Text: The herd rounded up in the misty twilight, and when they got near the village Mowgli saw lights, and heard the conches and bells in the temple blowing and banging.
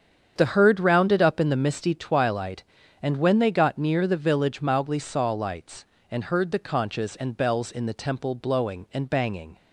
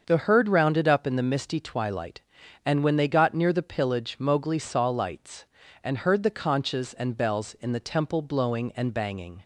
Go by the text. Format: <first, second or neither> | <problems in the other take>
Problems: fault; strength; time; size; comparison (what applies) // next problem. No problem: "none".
first | starts louder than the rest; until 1.0 s; 6.5 dB; strong in the first // says "pillage" for "village"; at 3.6 s